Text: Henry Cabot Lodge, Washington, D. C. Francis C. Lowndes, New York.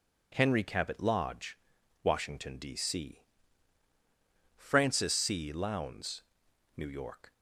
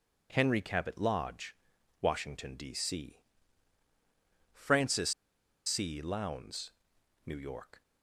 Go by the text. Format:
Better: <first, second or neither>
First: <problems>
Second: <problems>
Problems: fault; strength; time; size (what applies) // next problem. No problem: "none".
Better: first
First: pauses between "C" and "Francis"; strong; at 3.2 s; 1.3 s long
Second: pauses between "C" and "Francis"; strong; at 3.1 s; 1.3 s long // pauses between "Francis" and "C"; noticeable; at 5.1 s; 0.55 s long